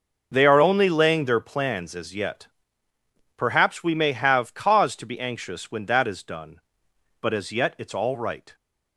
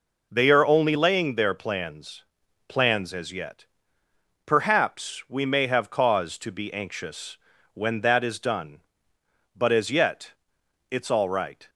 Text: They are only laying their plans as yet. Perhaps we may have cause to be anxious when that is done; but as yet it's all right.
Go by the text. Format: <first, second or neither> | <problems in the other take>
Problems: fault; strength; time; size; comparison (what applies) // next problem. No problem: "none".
first | says "plans" twice; at 2.6 s // pauses between "anxious" and "when"; slight; at 7.3 s; 0.36 s long // pauses between "yet" and "it's"; noticeable; at 10.3 s; 0.58 s long